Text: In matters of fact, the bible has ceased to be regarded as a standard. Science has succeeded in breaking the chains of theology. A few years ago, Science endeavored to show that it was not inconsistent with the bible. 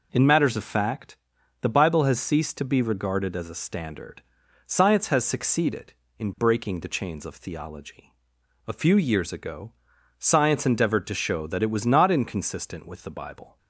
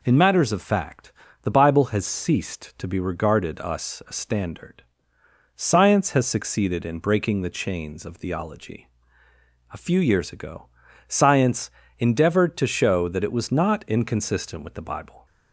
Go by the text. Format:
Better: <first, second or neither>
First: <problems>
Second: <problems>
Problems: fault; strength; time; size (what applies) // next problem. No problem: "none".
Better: first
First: none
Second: says "us" for "as"; at 3.5 s // pauses between "Science" and "endeavored"; slight; at 11.7 s; 0.26 s long